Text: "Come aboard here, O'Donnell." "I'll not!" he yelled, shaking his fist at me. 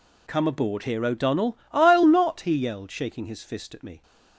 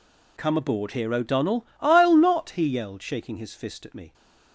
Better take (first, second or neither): neither